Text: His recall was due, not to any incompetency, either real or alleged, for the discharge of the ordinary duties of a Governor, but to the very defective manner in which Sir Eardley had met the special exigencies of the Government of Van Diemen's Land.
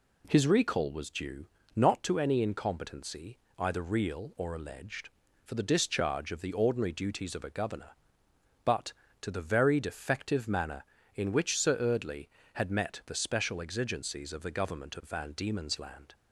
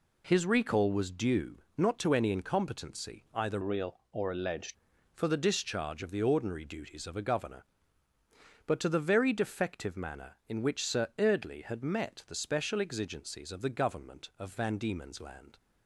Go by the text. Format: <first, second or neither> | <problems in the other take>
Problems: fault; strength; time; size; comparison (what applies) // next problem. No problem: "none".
first | changes voice from "real" to "alleged"; from 3.6 to 4.7 s; 1.1 s long